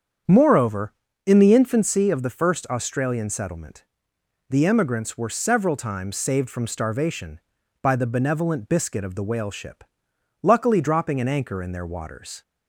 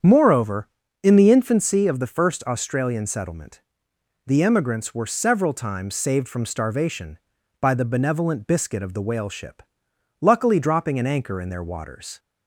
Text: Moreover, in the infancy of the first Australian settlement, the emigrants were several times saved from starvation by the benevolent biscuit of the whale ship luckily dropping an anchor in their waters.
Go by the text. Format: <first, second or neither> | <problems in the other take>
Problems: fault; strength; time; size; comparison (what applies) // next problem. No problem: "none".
neither | starts louder than the rest; strong; the same in both // pauses between "ship" and "luckily"; noticeable; the same in both